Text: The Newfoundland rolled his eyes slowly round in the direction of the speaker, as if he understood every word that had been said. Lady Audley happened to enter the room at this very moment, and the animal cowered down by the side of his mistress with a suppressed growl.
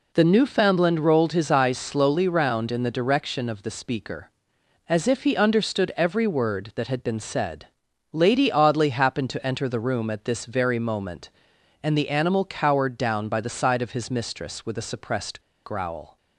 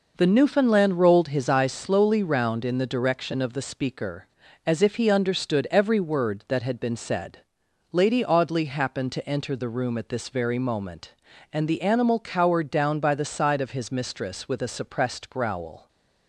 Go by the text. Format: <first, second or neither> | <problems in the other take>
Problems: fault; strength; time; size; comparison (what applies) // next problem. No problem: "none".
second | pauses between "suppressed" and "growl"; slight; at 15.4 s; 0.24 s long